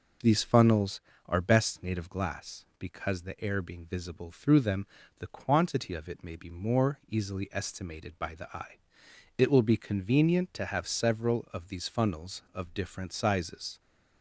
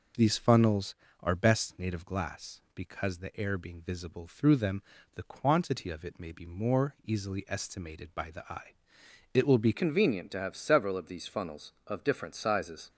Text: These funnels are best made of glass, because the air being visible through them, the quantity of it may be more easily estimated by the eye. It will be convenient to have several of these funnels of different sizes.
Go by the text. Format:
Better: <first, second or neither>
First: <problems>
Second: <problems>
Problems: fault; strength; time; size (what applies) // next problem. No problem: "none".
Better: first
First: none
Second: changes voice at "convenient"; from 9.7 s on; 3.1 s long